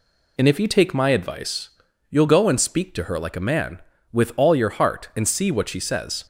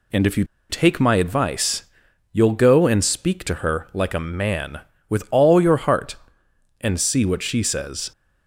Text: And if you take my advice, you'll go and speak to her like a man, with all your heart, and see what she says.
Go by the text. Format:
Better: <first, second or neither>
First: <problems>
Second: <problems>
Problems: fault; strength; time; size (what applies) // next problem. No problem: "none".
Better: first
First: none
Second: pauses between "you" and "take"; slight; at 0.4 s; 0.26 s long